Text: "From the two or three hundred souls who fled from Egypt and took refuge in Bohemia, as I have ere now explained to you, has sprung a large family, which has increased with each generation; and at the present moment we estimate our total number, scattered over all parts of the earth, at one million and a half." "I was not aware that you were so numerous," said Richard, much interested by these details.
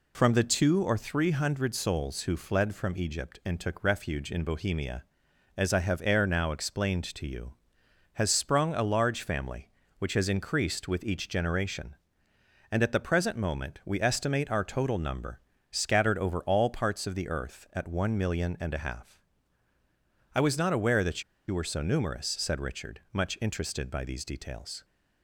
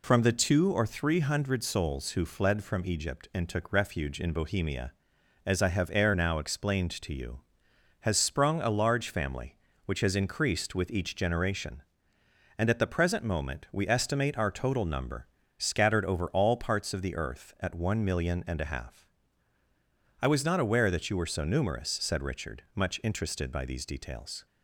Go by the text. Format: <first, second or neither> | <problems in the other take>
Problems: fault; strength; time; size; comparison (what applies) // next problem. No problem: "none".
second | pauses between "that" and "you"; slight; at 21.2 s; 0.25 s long